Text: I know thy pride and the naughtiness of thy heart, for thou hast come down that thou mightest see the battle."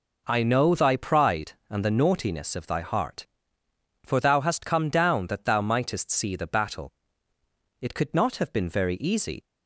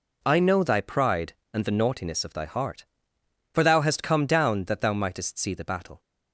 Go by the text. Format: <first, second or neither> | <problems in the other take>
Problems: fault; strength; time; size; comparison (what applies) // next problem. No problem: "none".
second | goes on to say "It could not have been very easy"; from 7.8 s on; 1.6 s long